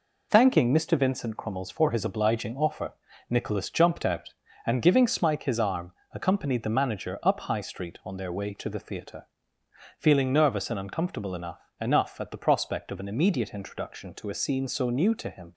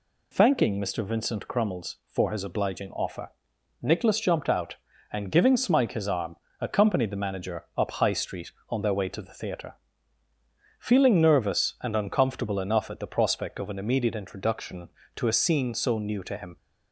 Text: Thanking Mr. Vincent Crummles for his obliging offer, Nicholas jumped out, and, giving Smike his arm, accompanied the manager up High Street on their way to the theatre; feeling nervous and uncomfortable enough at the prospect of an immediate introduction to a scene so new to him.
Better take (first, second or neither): second